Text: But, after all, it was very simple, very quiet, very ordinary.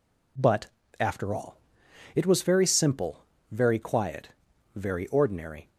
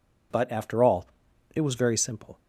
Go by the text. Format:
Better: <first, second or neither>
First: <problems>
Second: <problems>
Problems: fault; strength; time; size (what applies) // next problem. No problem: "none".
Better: first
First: none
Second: stops before "very quiet very ordinary"; at 2.3 s